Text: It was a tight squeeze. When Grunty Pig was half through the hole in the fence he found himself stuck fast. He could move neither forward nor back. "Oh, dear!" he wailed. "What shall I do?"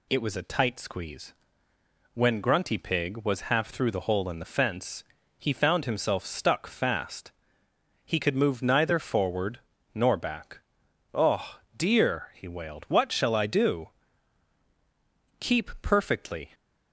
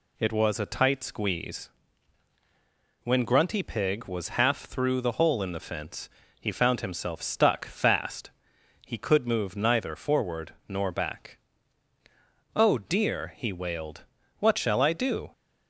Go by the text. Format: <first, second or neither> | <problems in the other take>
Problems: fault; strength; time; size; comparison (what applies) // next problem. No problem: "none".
second | pauses between "fence" and "he"; slight; at 5.0 s; 0.36 s long; slight in the second // pauses between "forward" and "nor"; slight; at 9.5 s; 0.34 s long; slight in the second // goes on to say "Keep perfectly"; noticeable; from 15.3 s on; 1.1 s long